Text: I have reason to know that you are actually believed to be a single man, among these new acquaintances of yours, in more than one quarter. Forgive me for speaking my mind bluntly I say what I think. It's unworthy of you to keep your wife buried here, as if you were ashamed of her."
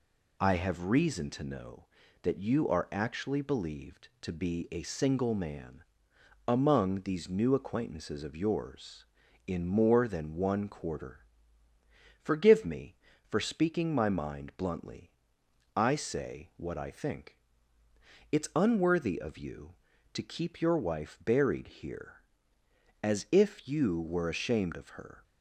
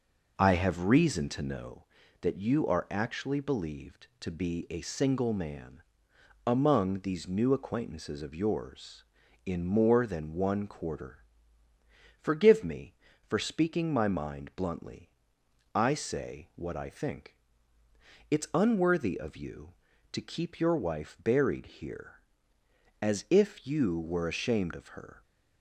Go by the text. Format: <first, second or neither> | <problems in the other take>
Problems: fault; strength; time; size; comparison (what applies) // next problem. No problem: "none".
first | starts louder than the rest; noticeable; until 1.8 s; 5 dB // pauses between "bluntly" and "I"; noticeable; at 15.0 s; 0.66 s long; noticeable in the first